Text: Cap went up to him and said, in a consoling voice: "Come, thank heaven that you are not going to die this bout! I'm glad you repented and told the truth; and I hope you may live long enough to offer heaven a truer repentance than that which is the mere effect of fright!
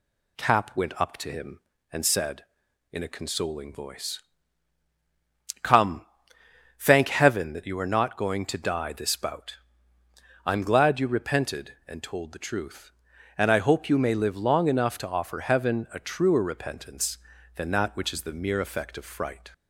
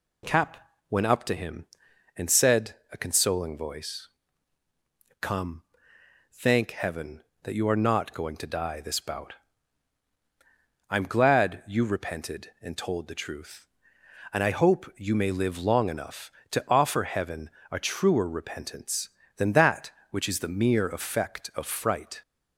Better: first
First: none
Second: pauses between "Cap" and "went"; slight; at 0.5 s; 0.32 s long // skips "in"; at 2.8 s // pauses between "heaven" and "a"; slight; at 17.4 s; 0.22 s long

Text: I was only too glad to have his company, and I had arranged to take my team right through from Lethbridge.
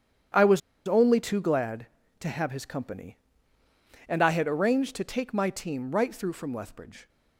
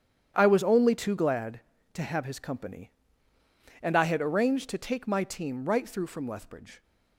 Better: second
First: starts louder than the rest; strong; until 1.6 s; 9.5 dB // pauses between "was" and "only"; slight; at 0.6 s; 0.28 s long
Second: starts louder than the rest; strong; until 1.3 s; 9.5 dB

